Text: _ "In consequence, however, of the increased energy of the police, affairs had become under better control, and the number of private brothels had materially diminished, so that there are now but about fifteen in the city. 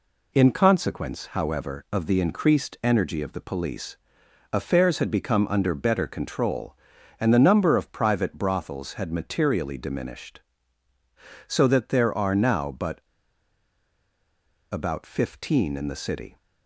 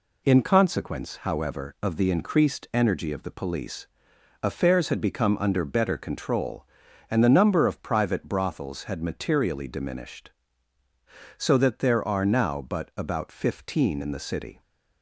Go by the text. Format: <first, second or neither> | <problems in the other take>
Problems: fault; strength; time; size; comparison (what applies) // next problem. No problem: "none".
second | pauses between "but" and "about"; strong; at 13.0 s; 1.6 s long